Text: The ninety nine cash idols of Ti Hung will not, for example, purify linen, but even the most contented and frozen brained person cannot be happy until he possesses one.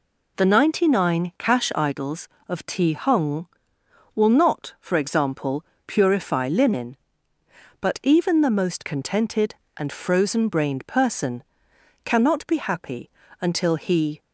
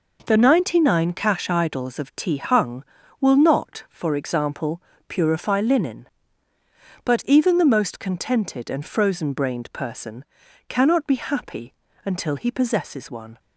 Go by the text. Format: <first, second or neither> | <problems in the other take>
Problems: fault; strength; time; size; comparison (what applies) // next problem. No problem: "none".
second | pauses between "person" and "cannot"; noticeable; at 11.4 s; 0.58 s long; noticeable in the second // pauses between "happy" and "until"; slight; at 13.0 s; 0.32 s long; slight in the second // stops before "possesses one"; at 14.2 s